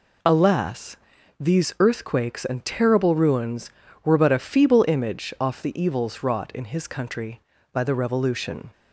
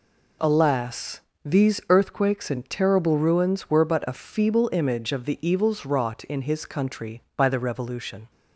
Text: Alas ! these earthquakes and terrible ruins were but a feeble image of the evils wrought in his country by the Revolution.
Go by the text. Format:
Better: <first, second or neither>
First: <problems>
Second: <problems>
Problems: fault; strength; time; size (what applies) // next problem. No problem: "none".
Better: second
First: says "off" for "of"; at 5.4 s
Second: none